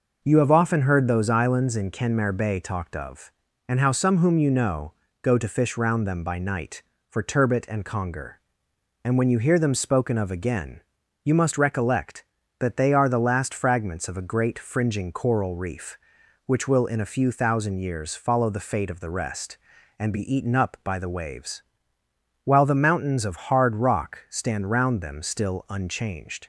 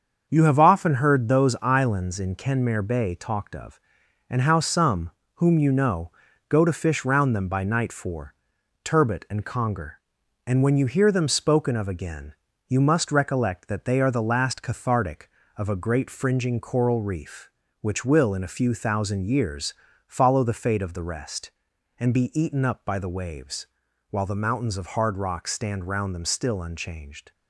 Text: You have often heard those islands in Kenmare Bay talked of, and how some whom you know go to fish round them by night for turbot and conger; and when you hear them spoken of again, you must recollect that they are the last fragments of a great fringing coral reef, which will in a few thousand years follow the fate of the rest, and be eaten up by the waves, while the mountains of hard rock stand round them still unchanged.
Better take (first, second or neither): first